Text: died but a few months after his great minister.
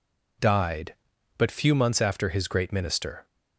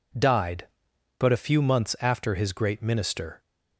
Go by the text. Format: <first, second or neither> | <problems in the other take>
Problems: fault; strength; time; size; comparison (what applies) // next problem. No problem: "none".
second | skips "a"; at 1.5 s